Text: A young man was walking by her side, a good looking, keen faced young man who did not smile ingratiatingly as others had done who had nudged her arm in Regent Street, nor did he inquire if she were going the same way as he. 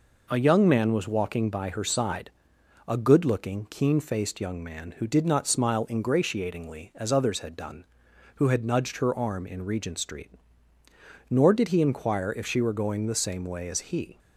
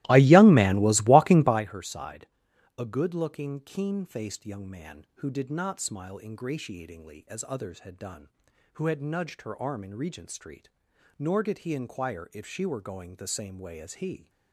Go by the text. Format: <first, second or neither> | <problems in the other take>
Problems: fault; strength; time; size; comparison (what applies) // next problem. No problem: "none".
first | starts louder than the rest; strong; until 1.6 s; 17 dB